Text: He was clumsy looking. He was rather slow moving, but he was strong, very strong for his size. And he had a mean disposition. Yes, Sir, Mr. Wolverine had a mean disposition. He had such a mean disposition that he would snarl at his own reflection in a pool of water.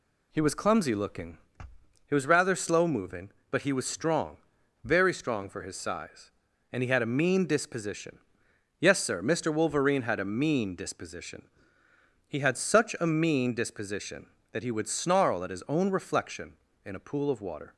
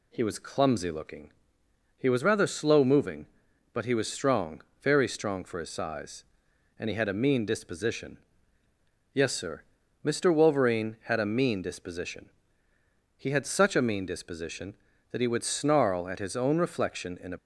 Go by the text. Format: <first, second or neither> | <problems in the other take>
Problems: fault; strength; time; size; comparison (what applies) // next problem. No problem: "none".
first | stops before "pool of water"; at 17.3 s